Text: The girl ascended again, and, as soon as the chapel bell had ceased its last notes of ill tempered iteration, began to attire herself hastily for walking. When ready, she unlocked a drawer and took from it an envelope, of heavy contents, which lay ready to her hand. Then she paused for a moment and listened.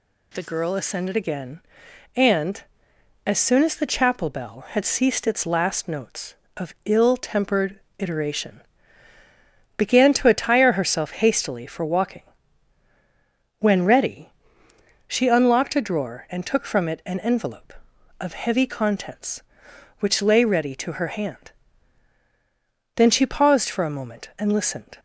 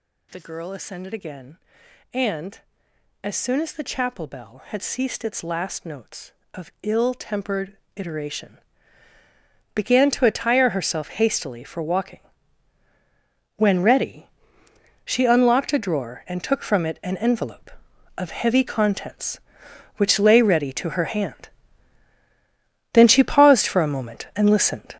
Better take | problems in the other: first | gets louder; strong; throughout; 9 dB // pauses between "tempered" and "iteration"; slight; at 7.7 s; 0.18 s long; slight in the first

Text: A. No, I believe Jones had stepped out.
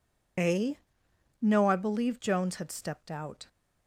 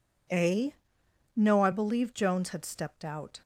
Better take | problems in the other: second | loses the start of "A"; at 0.3 s; 45 ms

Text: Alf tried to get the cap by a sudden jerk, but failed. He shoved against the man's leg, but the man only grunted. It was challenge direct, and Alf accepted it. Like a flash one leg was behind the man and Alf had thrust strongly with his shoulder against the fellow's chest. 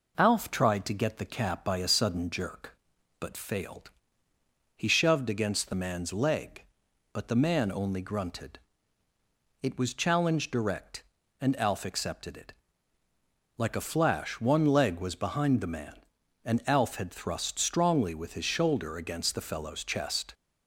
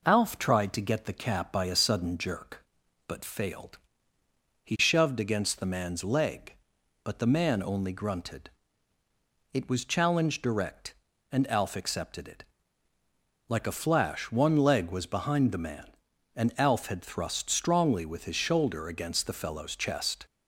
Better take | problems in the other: neither | none

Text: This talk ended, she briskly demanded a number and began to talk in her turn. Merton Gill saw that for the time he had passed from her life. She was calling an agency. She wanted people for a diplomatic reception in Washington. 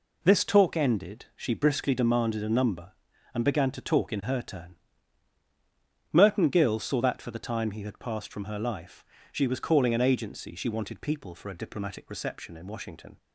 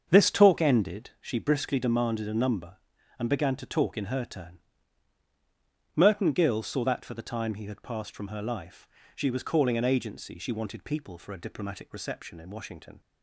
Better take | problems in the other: first | starts louder than the rest; until 1.1 s; 7 dB

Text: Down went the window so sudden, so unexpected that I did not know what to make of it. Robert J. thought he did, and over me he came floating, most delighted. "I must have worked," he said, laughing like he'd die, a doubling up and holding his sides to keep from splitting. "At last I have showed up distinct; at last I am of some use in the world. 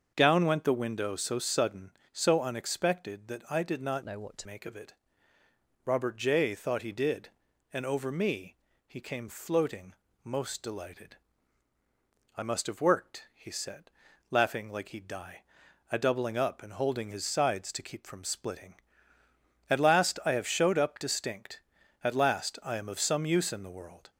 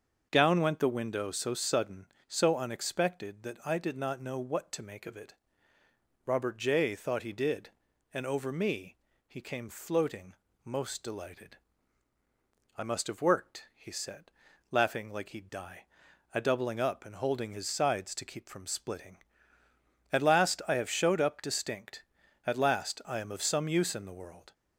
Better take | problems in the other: second | starts louder than the rest; until 1.1 s; 6.5 dB; also in the second // changes voice from "know" to "to"; from 4.0 to 4.4 s; 0.4 s long // pauses between "me" and "he"; slight; at 8.5 s; 0.30 s long; slight in the second

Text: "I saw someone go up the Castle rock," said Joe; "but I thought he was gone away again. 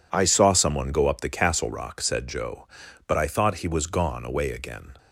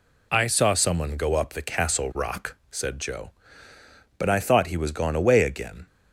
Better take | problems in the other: neither | none

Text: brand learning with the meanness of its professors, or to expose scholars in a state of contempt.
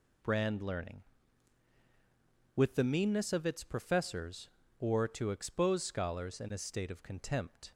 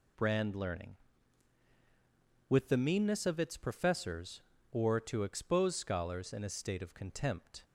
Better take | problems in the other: neither | none

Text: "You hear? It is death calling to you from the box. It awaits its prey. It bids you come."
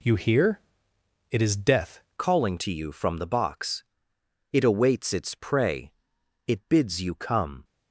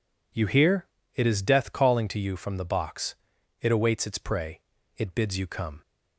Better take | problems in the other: second | changes voice at "calling"; from 2.1 s on; 5.5 s long

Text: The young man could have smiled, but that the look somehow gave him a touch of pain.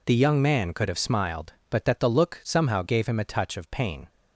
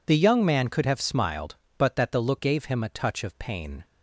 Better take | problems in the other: first | skips "somehow"; at 2.3 s

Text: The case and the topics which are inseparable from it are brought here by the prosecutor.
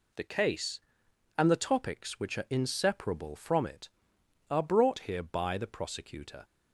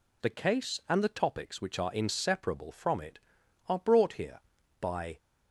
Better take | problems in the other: first | stops before "the prosecutor"; at 5.1 s

